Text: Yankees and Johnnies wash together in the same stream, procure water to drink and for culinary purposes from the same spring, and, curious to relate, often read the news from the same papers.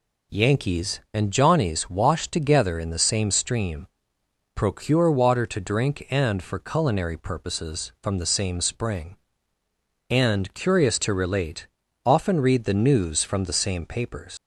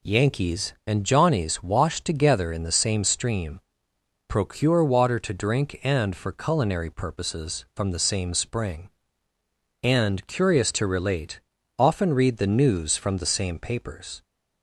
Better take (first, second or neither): second